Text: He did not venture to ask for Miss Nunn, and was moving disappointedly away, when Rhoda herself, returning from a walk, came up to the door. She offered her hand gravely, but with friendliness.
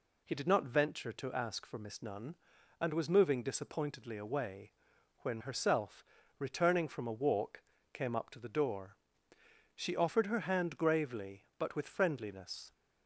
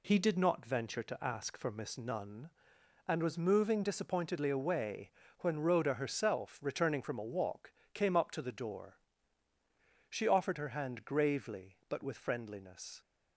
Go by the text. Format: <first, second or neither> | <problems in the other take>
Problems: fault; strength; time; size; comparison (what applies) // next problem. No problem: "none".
second | skips "Rhoda"; at 5.4 s